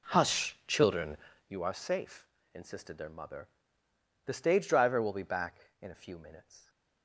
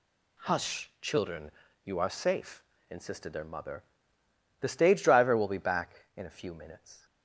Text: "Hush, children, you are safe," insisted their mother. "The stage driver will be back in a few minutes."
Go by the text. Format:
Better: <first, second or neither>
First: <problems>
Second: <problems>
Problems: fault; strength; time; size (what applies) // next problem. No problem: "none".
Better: second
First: starts louder than the rest; until 1.6 s; 3.5 dB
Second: none